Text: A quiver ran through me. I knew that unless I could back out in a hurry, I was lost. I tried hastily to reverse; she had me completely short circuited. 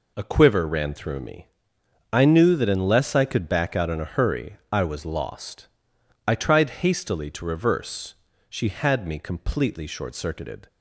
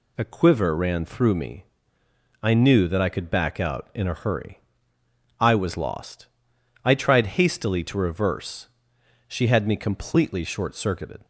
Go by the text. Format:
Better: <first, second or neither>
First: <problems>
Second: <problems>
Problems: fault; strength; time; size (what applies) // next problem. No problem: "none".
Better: first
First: none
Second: skips "unless"; at 3.0 s